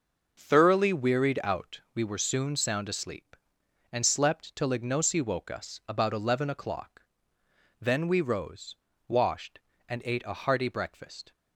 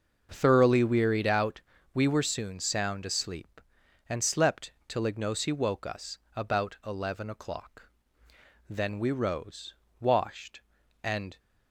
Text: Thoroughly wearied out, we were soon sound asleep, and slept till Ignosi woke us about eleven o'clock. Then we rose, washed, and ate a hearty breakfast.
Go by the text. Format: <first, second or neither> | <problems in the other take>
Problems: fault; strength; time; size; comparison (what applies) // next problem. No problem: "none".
first | starts louder than the rest; noticeable; until 1.3 s; 6 dB // pauses between "slept" and "till"; slight; at 4.7 s; 0.16 s long // pauses between "us" and "about"; slight; at 6.1 s; 0.18 s long // stops before "ate a hearty breakfast"; at 11.3 s